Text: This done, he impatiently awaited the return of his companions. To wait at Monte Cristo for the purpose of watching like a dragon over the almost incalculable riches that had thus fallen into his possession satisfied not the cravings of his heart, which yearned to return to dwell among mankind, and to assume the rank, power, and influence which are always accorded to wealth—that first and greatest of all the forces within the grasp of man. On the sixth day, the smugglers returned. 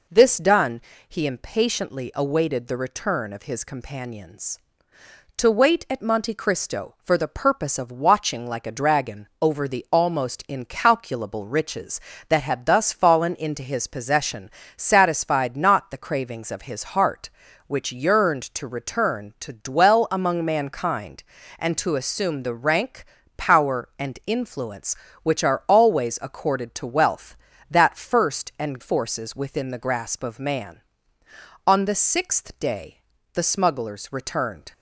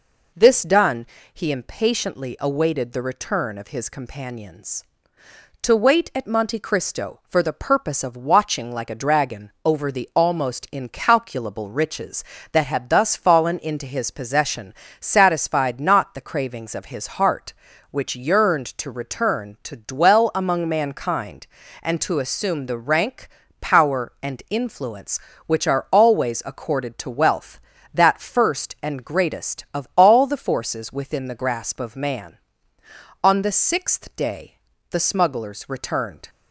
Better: second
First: pauses between "possession" and "satisfied"; slight; at 14.4 s; 0.28 s long // skips "greatest of all the"; at 28.7 s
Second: pauses between "possession" and "satisfied"; slight; at 14.7 s; 0.28 s long

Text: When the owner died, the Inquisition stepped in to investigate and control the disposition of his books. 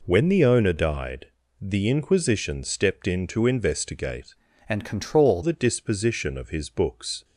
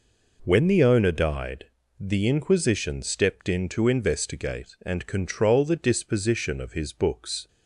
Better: second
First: changes voice from "and" to "control"; from 4.6 to 5.4 s; 0.8 s long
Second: none

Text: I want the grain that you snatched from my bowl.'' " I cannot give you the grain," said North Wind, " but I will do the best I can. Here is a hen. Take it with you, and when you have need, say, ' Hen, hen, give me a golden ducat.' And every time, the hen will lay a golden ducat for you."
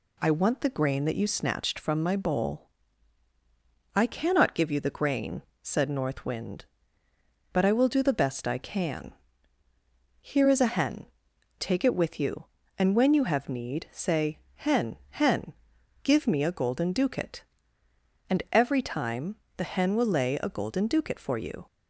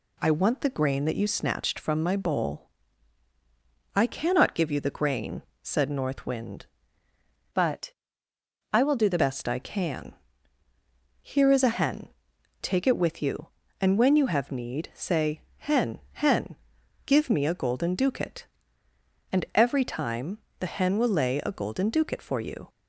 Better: first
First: none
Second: changes voice from "but" to "the"; from 7.5 to 9.1 s; 1.6 s long // pauses between "but" and "I"; noticeable; at 7.9 s; 0.78 s long

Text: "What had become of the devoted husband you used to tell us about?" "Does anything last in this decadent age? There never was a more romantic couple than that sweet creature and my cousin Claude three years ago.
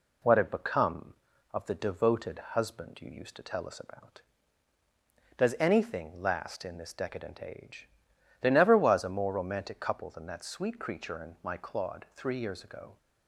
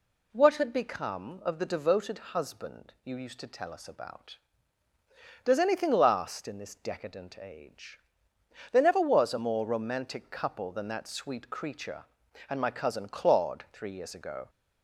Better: second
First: skips "cousin"; at 11.5 s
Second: none

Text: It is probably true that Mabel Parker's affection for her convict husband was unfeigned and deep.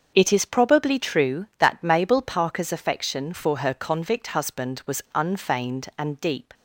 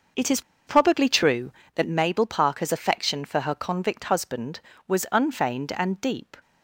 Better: first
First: starts louder than the rest; until 1.1 s; 6.5 dB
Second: starts louder than the rest; noticeable; until 1.4 s; 6 dB // pauses between "is" and "probably"; slight; at 0.4 s; 0.26 s long

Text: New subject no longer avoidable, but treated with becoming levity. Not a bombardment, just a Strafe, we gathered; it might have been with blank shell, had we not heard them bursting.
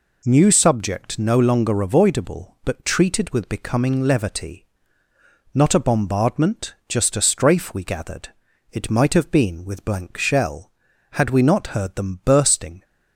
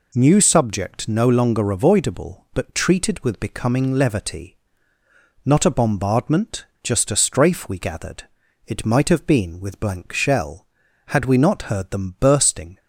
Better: neither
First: none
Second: none

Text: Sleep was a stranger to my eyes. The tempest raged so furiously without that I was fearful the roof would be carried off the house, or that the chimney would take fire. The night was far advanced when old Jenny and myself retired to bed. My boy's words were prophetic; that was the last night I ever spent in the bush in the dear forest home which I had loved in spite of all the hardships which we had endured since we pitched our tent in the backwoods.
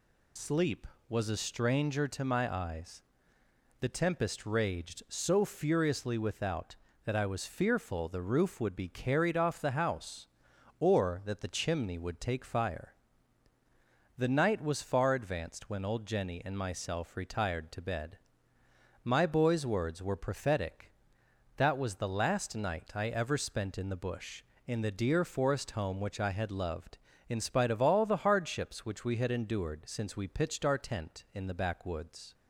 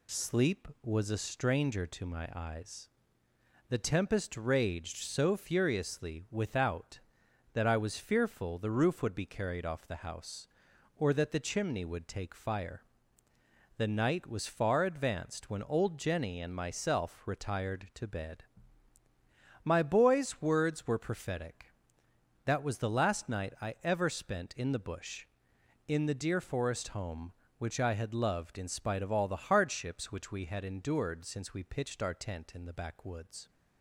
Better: second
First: loses the start of "Sleep"; at 0.3 s; 50 ms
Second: none

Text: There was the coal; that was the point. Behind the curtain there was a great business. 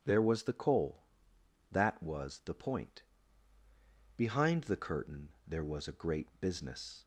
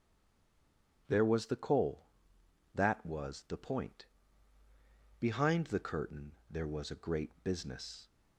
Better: first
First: starts louder than the rest; strong; until 1.0 s; 9 dB // pauses between "curtain" and "there"; slight; at 5.2 s; 0.18 s long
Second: stays silent before the first word; until 1.0 s; 1.0 s long // starts louder than the rest; strong; until 2.0 s; 9 dB // pauses between "curtain" and "there"; slight; at 6.3 s; 0.18 s long

